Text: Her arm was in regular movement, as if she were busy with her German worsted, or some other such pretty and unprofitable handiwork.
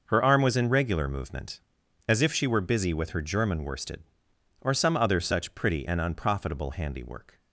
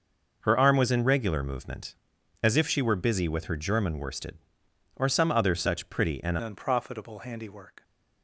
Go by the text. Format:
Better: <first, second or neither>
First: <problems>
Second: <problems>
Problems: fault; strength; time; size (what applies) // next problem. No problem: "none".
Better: first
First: none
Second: changes voice at "unprofitable"; from 6.4 s on; 1.4 s long